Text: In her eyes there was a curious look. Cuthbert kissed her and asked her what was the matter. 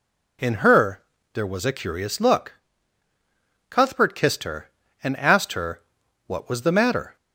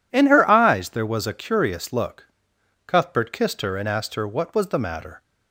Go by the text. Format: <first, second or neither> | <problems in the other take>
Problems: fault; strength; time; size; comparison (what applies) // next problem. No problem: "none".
second | skips "eyes"; at 1.1 s // pauses between "her" and "what"; noticeable; at 5.8 s; 0.46 s long